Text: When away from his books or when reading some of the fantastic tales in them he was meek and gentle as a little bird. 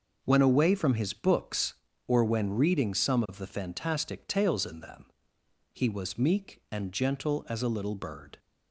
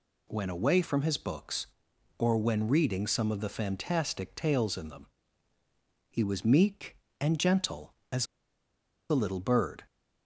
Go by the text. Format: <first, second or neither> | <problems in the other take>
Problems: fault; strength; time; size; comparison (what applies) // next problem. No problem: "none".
first | pauses between "them" and "he"; at 5.0 s; 1.0 s long; noticeable in the first // pauses between "as" and "a"; noticeable; at 8.2 s; 0.84 s long